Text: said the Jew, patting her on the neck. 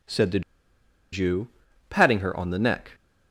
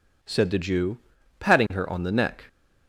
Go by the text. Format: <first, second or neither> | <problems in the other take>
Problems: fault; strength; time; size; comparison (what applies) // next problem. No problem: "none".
second | pauses between "the" and "Jew"; noticeable; at 0.4 s; 0.72 s long